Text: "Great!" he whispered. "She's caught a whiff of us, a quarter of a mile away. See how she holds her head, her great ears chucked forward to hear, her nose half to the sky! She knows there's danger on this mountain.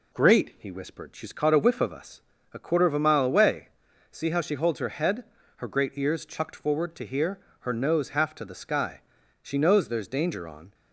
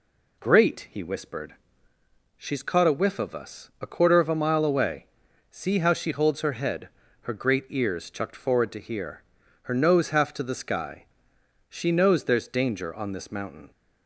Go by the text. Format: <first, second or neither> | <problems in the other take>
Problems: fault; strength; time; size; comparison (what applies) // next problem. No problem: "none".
second | stops before "this mountain"; at 10.7 s